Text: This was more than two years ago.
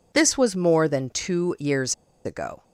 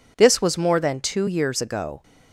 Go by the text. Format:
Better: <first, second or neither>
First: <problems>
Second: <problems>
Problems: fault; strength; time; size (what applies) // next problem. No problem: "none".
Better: second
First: pauses between "years" and "ago"; slight; at 1.9 s; 0.30 s long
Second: none